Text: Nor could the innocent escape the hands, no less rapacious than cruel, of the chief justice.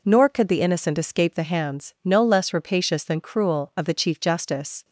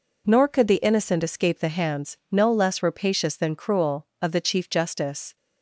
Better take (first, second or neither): neither